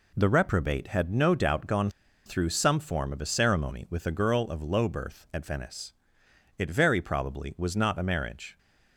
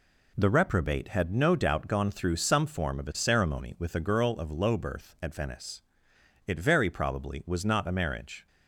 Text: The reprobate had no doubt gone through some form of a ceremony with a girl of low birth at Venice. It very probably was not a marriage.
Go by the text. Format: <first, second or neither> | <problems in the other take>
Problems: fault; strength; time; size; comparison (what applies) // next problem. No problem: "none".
second | pauses between "gone" and "through"; slight; at 1.8 s; 0.36 s long